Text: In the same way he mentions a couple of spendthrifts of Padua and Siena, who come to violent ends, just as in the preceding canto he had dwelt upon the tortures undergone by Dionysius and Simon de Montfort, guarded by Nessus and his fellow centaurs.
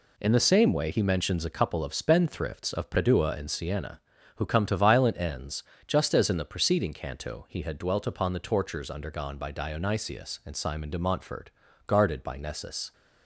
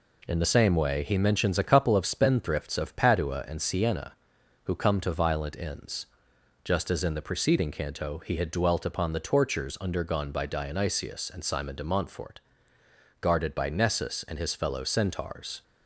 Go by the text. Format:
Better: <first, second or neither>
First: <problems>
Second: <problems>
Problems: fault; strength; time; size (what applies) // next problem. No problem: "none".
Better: second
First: stops before "and his fellow centaurs"; at 12.9 s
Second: none